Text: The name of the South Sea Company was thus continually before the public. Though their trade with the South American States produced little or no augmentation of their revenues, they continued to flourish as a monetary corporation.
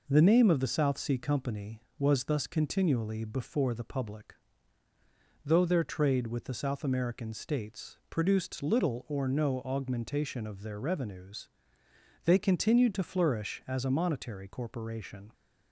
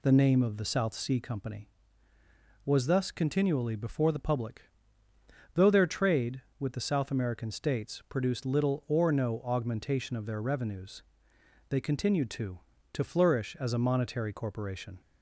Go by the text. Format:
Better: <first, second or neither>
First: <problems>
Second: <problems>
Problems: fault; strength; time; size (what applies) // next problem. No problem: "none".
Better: first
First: none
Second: says "to" twice; at 12.9 s